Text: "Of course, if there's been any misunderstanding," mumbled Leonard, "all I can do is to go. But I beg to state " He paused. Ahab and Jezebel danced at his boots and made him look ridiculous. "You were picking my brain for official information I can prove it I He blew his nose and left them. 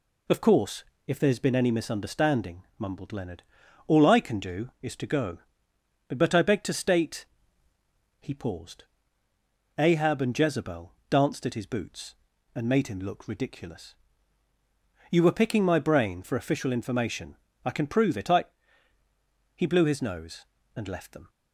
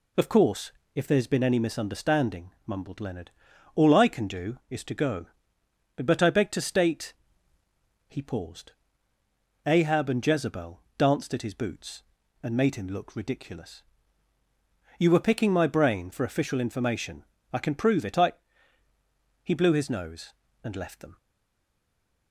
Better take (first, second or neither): first